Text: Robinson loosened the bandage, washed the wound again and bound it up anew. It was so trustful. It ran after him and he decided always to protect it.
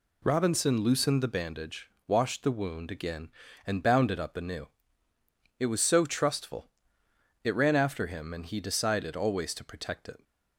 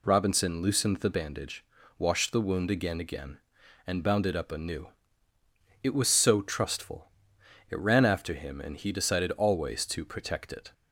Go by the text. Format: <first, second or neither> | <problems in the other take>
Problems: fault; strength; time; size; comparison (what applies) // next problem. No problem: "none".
first | says "again" twice; at 3.0 s